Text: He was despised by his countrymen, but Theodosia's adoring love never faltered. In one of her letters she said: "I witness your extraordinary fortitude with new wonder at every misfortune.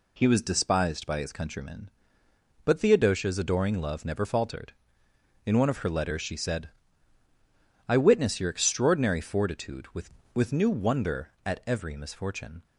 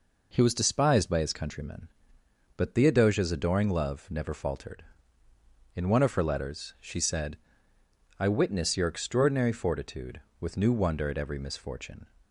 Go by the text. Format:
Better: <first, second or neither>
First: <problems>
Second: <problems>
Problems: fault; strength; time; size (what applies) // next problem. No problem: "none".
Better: second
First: says "with" twice; at 10.3 s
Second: none